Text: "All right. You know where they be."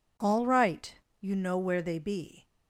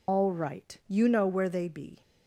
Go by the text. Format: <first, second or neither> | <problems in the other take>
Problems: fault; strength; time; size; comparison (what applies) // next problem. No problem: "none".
first | loses the start of "All"; at 0.0 s; 120 ms